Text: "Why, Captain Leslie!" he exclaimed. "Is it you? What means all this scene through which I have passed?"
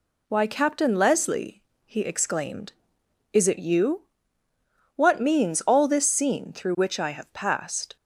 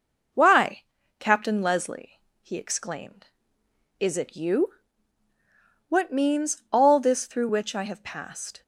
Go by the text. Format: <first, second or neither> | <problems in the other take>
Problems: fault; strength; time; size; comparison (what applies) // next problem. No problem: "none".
first | skips "scene"; at 7.2 s